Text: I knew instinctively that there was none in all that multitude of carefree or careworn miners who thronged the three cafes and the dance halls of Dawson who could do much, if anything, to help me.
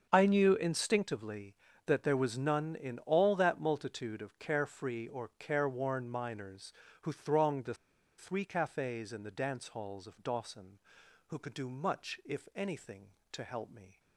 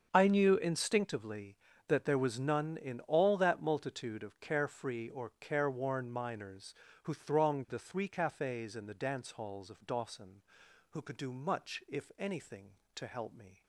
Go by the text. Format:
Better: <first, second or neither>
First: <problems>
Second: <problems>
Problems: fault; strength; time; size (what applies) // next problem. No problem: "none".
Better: second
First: starts louder than the rest; until 1.1 s; 6.5 dB // pauses between "the" and "three"; at 7.7 s; 0.44 s long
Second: starts louder than the rest; until 1.1 s; 6.5 dB